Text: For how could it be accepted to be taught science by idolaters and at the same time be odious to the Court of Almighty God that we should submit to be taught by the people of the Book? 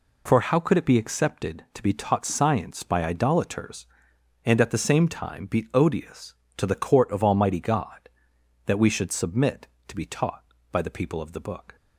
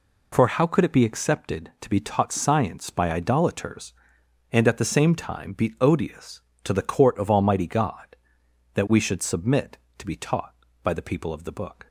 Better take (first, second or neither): neither